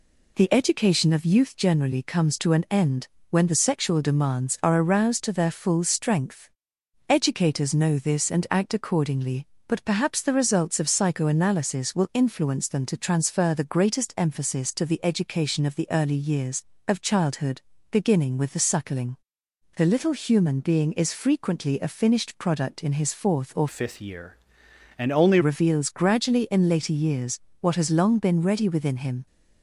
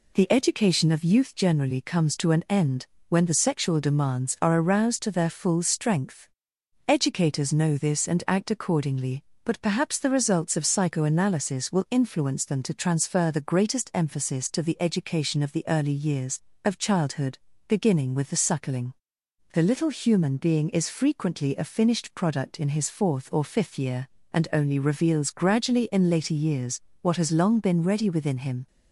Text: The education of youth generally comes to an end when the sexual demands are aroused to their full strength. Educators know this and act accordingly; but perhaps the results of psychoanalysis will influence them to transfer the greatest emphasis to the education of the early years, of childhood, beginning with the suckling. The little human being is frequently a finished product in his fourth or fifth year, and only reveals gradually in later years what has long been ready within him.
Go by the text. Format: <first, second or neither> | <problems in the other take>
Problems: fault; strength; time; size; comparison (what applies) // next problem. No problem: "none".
second | pauses between "end" and "when"; slight; at 3.0 s; 0.22 s long; slight in the second // changes voice from "fifth" to "only"; from 23.6 to 25.3 s; 1.7 s long // pauses between "years" and "what"; slight; at 27.3 s; 0.20 s long; slight in the second